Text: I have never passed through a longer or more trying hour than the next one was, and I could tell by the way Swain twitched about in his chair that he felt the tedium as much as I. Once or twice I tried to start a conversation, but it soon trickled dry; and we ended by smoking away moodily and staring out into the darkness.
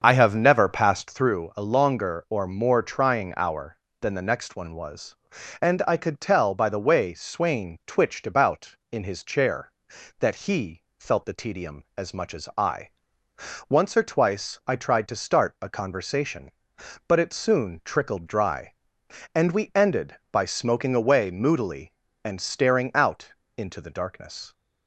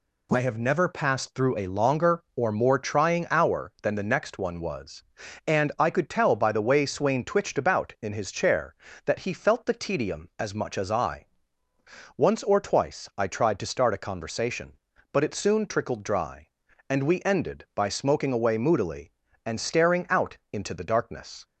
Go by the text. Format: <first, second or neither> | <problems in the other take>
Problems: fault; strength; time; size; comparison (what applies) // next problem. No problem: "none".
second | starts louder than the rest; until 1.3 s; 7 dB // pauses between "he" and "felt"; slight; at 10.8 s; 0.16 s long // pauses between "out" and "into"; slight; at 23.3 s; 0.22 s long; slight in the second